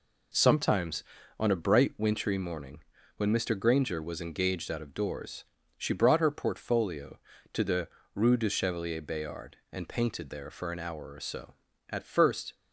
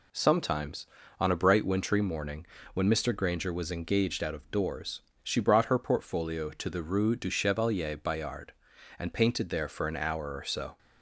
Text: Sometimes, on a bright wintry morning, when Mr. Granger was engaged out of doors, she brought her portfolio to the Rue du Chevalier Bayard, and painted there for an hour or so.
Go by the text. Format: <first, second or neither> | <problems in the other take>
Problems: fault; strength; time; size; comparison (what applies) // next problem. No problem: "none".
second | pauses between "the" and "Rue"; slight; at 7.8 s; 0.28 s long // goes on to say "At first"; noticeable; from 11.9 s on; 0.64 s long